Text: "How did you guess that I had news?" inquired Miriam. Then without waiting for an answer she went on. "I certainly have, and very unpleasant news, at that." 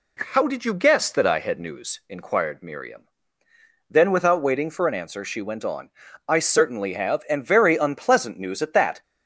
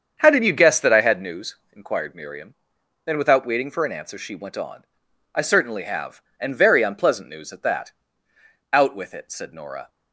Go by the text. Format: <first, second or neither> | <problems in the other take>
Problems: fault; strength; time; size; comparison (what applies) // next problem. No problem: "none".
first | starts louder than the rest; strong; until 1.2 s; 7.5 dB // goes on to say "Out with it said Nora"; noticeable; from 8.7 s on; 1.1 s long